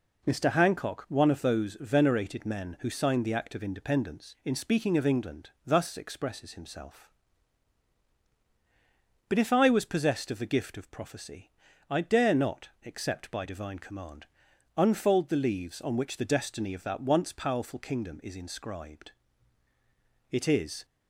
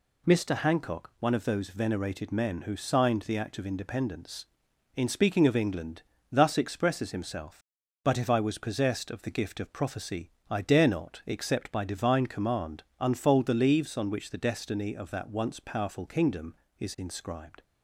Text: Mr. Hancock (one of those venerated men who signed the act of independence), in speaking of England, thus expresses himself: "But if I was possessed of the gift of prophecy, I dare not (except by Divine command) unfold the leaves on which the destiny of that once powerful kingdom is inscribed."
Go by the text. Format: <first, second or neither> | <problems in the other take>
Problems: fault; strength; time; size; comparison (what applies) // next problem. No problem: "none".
second | goes on to say "It is"; from 20.2 s on; 0.56 s long